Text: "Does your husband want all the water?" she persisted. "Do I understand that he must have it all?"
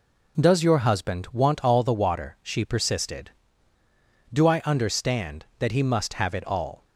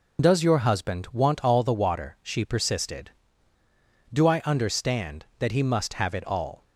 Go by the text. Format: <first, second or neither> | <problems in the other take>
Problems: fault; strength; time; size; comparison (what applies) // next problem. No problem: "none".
first | loses the start of "Does"; at 0.1 s; 30 ms